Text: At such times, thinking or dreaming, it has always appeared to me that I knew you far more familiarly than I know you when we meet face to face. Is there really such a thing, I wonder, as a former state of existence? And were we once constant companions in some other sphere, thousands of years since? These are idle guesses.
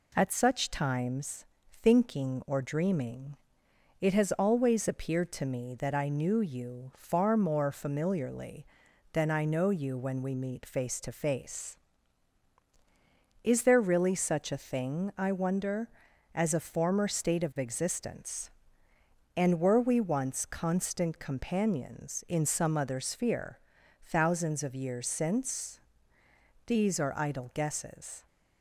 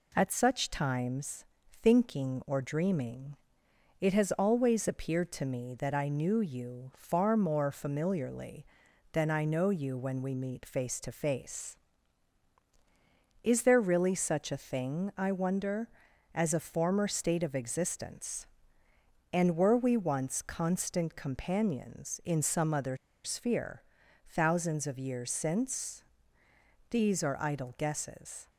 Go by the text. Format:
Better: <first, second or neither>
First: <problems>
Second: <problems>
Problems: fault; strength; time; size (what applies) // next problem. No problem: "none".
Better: first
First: none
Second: pauses between "other" and "sphere"; slight; at 22.9 s; 0.27 s long